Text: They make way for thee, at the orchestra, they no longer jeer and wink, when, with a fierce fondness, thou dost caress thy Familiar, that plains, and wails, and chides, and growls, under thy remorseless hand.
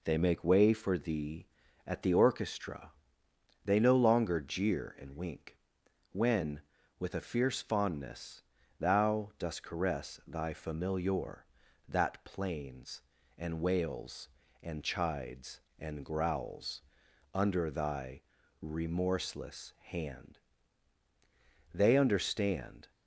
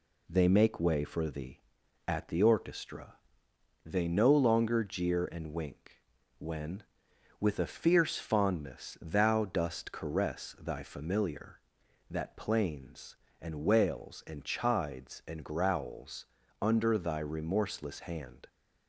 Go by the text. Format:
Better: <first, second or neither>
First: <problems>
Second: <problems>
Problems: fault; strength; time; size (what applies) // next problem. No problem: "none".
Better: second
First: pauses between "thy" and "remorseless"; at 18.2 s; 0.42 s long // goes on to say "They understand"; noticeable; from 21.7 s on; 1.1 s long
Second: none